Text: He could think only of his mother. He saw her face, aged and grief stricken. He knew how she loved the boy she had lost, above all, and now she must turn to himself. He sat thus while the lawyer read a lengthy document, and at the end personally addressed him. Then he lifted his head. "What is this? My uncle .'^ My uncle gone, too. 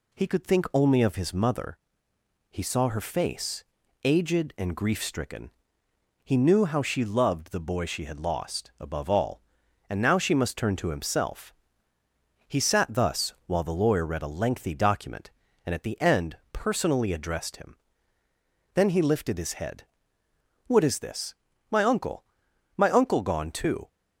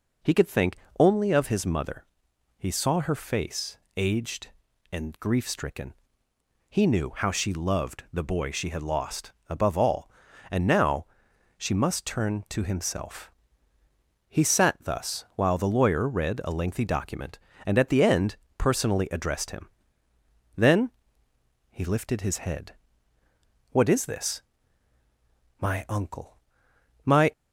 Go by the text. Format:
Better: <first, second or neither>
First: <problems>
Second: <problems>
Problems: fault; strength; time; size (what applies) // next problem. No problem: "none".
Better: first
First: pauses between "end" and "personally"; slight; at 16.3 s; 0.16 s long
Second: pauses between "think" and "only"; slight; at 0.7 s; 0.24 s long // pauses between "now" and "she"; noticeable; at 11.0 s; 0.52 s long // pauses between "end" and "personally"; slight; at 18.3 s; 0.22 s long // pauses between "Then" and "he"; noticeable; at 20.9 s; 0.78 s long // stops before "uncle gone too"; at 27.3 s